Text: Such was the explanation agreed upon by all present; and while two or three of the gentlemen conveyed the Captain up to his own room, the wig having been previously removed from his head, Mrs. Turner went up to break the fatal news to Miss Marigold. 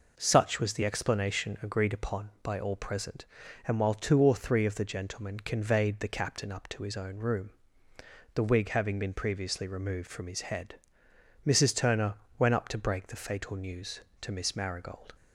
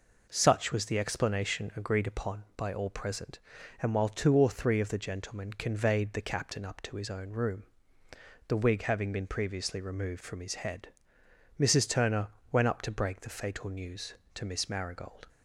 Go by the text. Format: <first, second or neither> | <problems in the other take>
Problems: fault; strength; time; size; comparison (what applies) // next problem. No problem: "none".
neither | pauses between "Turner" and "went"; slight; the same in both